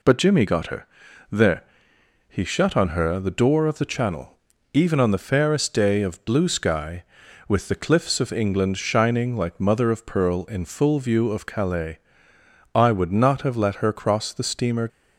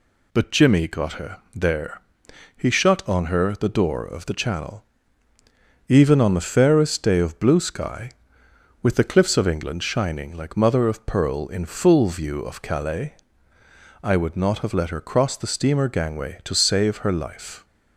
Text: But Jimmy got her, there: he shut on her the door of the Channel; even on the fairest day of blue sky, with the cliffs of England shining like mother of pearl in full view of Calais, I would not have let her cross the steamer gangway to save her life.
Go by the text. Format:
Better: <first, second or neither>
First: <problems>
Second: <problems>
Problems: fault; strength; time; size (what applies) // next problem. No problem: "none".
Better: second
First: stops before "gangway to save her life"; at 14.8 s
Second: none